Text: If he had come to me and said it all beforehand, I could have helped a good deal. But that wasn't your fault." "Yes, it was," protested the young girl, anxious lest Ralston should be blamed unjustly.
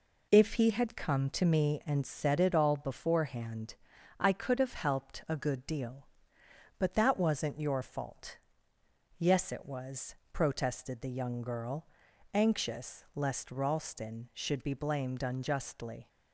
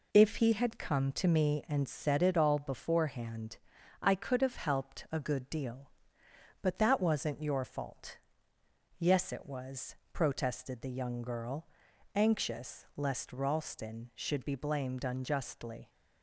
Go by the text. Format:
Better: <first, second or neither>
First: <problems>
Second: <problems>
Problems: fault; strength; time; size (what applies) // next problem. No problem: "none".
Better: neither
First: none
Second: none